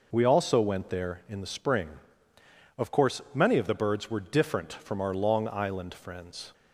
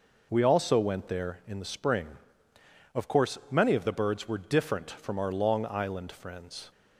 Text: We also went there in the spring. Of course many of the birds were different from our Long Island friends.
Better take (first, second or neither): neither